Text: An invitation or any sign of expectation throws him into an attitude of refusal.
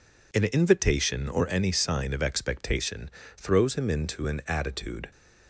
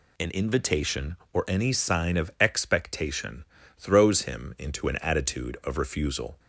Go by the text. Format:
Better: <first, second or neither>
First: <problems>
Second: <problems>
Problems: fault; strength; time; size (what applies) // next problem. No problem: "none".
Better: second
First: pauses between "expectation" and "throws"; slight; at 3.0 s; 0.28 s long // stops before "of refusal"; at 5.1 s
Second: pauses between "expectation" and "throws"; slight; at 3.4 s; 0.34 s long